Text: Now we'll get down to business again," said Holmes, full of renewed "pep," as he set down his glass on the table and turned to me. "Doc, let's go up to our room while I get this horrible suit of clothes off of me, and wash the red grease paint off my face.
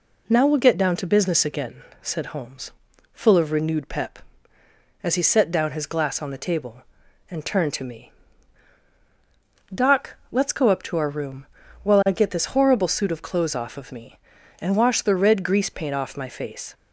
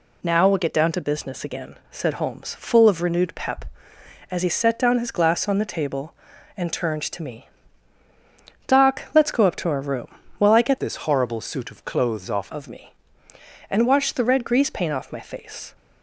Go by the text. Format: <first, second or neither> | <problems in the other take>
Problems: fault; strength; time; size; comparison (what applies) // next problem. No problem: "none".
first | pauses between "room" and "while"; slight; at 10.0 s; 0.32 s long; also in the first // changes voice from "this" to "off"; from 10.7 to 12.5 s; 1.8 s long